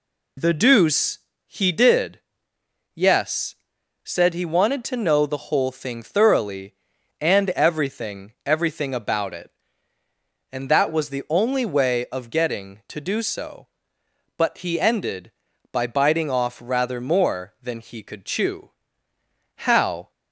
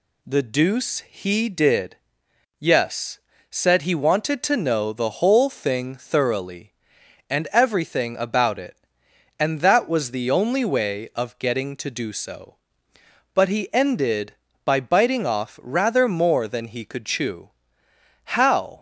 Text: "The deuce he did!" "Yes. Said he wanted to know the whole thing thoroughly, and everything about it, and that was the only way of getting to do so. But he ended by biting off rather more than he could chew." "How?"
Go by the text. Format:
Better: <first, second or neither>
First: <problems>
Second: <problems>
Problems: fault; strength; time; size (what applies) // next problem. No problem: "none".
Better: second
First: pauses between "deuce" and "he"; slight; at 1.1 s; 0.30 s long // says "everything" twice; at 8.4 s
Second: none